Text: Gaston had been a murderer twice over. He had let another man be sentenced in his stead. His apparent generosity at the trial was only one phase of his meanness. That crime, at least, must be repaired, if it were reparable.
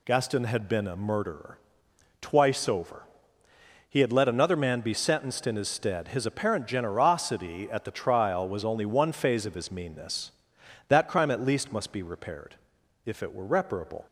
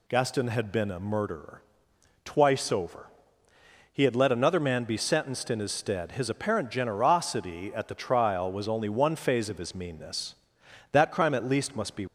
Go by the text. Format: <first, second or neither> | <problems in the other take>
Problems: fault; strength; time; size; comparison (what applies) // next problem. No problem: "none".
first | pauses between "murderer" and "twice"; noticeable; at 1.6 s; 0.62 s long; noticeable in the first // stops before "repaired if it were reparable"; at 12.0 s